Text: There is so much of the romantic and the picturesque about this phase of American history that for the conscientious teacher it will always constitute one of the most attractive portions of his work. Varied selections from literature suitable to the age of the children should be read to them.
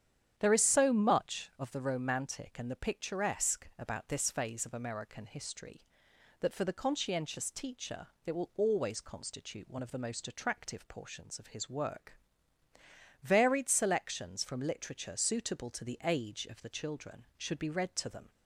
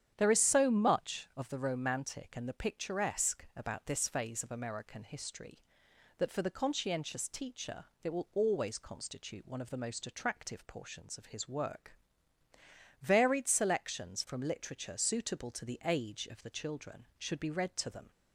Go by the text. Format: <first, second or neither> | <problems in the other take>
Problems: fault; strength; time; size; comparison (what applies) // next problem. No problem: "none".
neither | starts louder than the rest; strong; the same in both // pauses between "teacher" and "it"; slight; the same in both